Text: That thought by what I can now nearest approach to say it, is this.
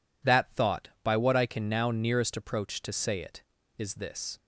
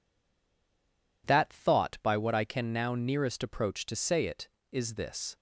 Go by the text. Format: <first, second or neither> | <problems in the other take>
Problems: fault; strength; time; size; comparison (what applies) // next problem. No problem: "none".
first | stays silent before the first word; noticeable; until 1.2 s; 1.2 s long